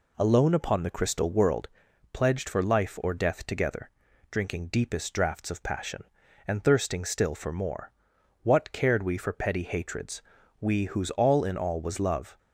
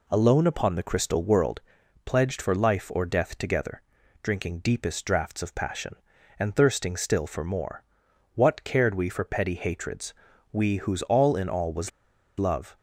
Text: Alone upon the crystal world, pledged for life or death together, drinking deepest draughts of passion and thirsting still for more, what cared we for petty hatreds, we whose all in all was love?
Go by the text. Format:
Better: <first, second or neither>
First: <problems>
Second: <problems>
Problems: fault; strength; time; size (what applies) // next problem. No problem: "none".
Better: first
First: none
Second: pauses between "was" and "love"; noticeable; at 11.9 s; 0.48 s long